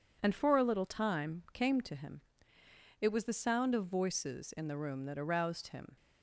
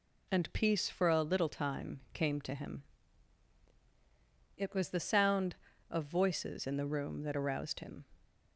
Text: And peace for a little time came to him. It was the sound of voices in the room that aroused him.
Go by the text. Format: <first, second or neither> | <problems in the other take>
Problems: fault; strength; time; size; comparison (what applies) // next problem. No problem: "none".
second | skips "peace"; at 0.3 s